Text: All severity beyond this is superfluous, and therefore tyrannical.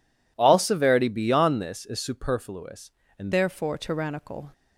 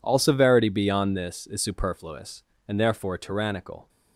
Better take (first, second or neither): second